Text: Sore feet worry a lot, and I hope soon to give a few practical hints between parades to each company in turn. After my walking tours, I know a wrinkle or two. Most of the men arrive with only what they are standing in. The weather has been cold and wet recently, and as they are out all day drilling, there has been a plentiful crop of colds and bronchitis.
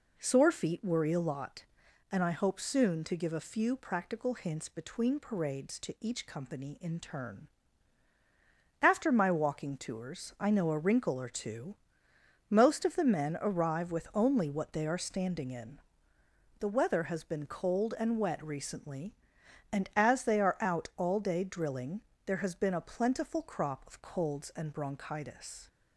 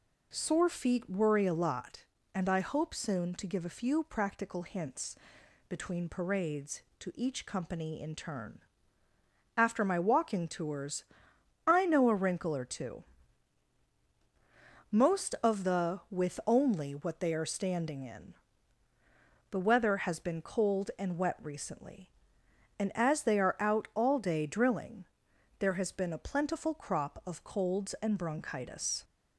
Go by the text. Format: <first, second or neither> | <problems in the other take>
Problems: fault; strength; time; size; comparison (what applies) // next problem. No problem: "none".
first | pauses between "hints" and "between"; noticeable; at 5.1 s; 0.54 s long // skips "men arrive"; at 16.0 s